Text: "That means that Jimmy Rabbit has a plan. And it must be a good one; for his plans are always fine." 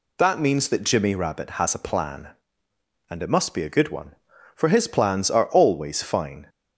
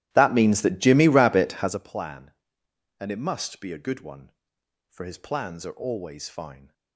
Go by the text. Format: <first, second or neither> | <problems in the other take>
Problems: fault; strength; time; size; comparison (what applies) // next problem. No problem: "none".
first | starts louder than the rest; strong; until 1.8 s; 14.5 dB